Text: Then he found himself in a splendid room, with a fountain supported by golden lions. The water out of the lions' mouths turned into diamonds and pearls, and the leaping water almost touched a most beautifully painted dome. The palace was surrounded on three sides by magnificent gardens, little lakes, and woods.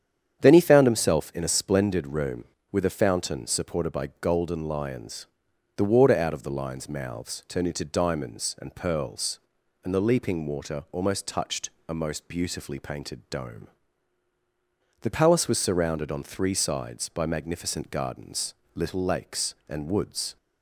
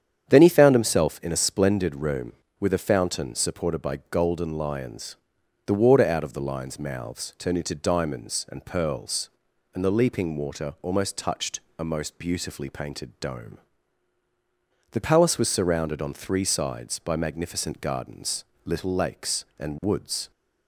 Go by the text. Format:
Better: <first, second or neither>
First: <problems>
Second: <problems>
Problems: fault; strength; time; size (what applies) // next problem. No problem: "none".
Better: neither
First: starts louder than the rest; strong; until 1.4 s; 9 dB // pauses between "touched" and "a"; slight; at 11.7 s; 0.18 s long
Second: starts louder than the rest; strong; until 1.3 s; 8.5 dB // pauses between "touched" and "a"; slight; at 11.6 s; 0.18 s long